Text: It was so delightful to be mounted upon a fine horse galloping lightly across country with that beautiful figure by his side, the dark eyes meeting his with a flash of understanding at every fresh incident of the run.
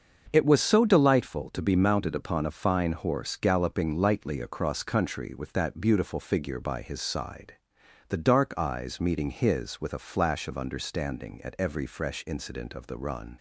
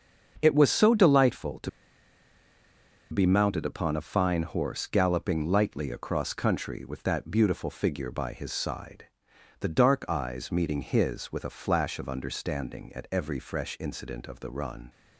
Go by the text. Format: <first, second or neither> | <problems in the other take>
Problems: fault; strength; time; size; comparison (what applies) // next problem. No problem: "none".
first | starts louder than the rest; until 1.4 s; 7 dB; also in the first // pauses between "to" and "be"; strong; at 1.6 s; 1.4 s long